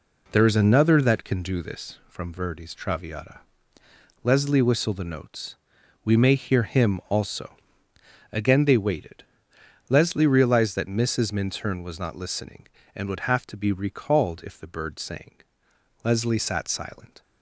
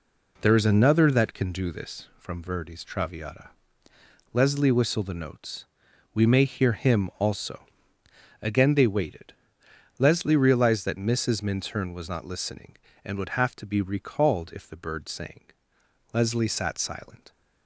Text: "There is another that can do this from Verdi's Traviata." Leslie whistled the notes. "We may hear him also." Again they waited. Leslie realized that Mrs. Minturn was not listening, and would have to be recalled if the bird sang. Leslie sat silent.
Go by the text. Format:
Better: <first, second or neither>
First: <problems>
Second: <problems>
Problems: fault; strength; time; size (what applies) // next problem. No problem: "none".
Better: neither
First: none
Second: none